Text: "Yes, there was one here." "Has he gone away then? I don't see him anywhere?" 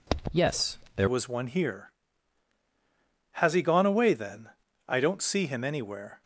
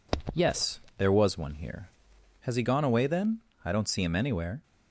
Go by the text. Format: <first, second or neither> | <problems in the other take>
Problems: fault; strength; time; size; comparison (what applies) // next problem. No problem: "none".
second | changes voice at "was"; from 1.0 s on; 5.2 s long